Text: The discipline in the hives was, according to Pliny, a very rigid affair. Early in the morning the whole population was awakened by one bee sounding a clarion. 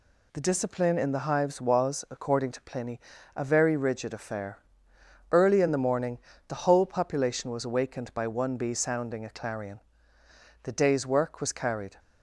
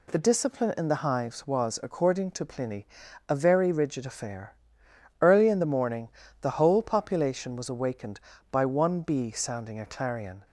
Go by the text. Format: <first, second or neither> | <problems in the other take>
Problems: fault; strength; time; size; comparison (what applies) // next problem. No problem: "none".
second | pauses between "morning" and "the"; slight; at 6.1 s; 0.30 s long; slight in the second // goes on to say "The day's work was carried"; from 10.6 s on; 1.3 s long